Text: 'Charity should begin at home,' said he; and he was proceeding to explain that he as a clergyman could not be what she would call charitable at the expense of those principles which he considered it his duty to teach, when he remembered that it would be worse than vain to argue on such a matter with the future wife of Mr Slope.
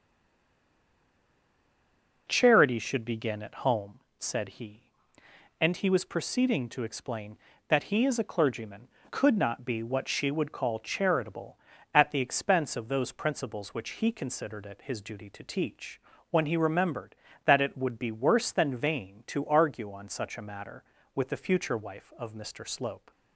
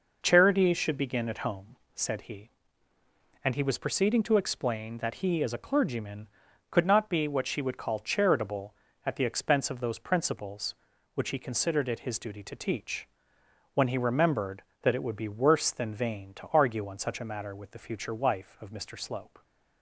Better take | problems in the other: second | stays silent before the first word; until 2.2 s; 2.2 s long

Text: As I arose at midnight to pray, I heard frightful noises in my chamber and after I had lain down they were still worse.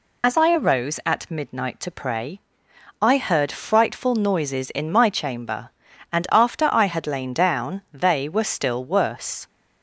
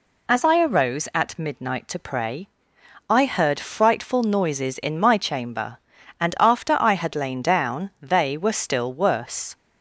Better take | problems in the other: second | loses the start of "As"; at 0.2 s; 30 ms

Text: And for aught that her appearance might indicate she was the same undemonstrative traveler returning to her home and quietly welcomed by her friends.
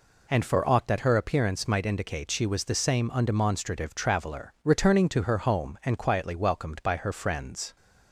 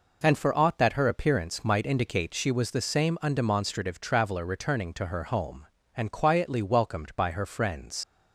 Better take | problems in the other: first | leaves "friends" unfinished; at 8.0 s; 105 ms

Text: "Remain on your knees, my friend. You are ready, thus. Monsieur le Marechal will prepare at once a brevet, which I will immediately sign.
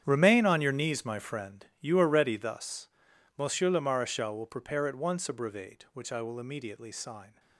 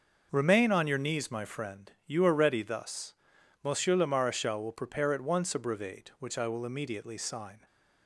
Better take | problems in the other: second | gets quieter; strong; throughout; 15 dB // starts louder than the rest; strong; until 1.0 s; 9.5 dB; also in the second

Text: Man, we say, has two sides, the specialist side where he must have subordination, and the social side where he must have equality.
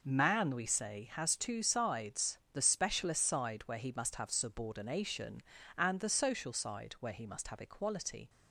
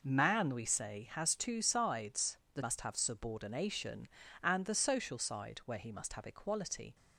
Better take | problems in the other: first | skips "specialist side where he"; at 2.6 s

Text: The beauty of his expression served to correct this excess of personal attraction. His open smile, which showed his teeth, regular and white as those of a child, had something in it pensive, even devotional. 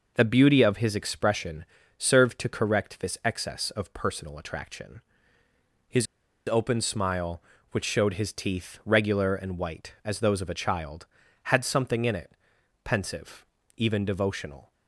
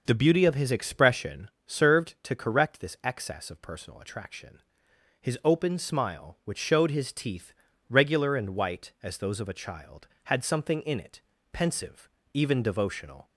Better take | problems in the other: second | pauses between "expression" and "served"; slight; at 1.6 s; 0.34 s long; slight in the second // pauses between "His" and "open"; at 6.0 s; 0.42 s long // pauses between "it" and "pensive"; noticeable; at 12.3 s; 0.52 s long; slight in the second

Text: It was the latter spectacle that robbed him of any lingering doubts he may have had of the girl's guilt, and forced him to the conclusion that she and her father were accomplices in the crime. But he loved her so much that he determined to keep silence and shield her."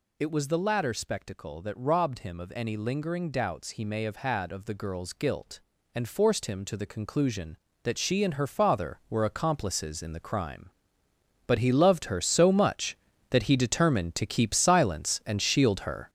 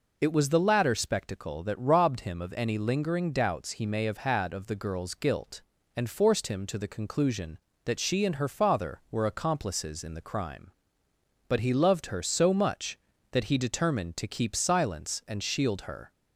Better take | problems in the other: second | gets louder; strong; throughout; 7.5 dB

